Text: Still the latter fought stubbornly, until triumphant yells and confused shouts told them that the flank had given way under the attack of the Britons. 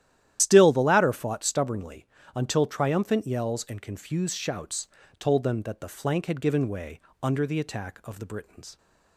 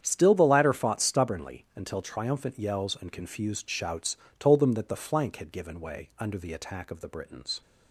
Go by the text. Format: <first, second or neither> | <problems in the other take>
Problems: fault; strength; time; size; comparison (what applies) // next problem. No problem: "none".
second | loses the start of "Still"; at 0.3 s; 90 ms // starts louder than the rest; strong; until 1.4 s; 12 dB; strong in the second // pauses between "shouts" and "told"; slight; at 4.8 s; 0.32 s long; slight in the second // pauses between "way" and "under"; slight; at 6.9 s; 0.24 s long